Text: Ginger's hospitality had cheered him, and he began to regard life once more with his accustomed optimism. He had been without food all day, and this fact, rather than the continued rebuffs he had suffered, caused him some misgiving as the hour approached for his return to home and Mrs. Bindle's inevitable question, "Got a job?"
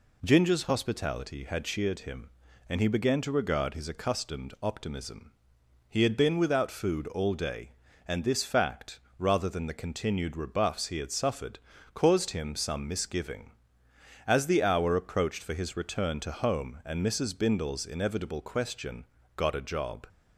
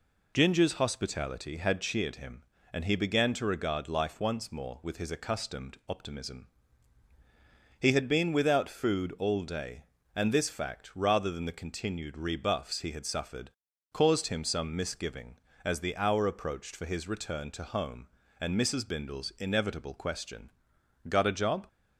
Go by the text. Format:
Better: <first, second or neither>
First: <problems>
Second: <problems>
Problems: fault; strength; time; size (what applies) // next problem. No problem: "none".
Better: second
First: skips "life once more with"; at 3.7 s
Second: none